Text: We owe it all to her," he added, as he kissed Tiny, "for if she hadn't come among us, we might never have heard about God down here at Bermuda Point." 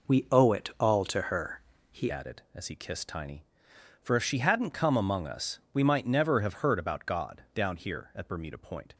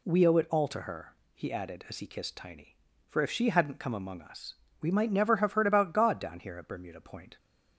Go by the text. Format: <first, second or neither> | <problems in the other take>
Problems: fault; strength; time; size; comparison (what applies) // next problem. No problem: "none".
second | changes voice at "added"; from 2.1 s on; 6.8 s long